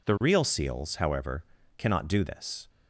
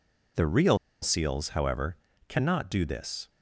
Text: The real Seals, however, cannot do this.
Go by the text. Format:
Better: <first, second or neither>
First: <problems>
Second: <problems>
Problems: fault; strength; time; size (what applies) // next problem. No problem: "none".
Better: first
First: none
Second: pauses between "real" and "Seals"; slight; at 0.7 s; 0.24 s long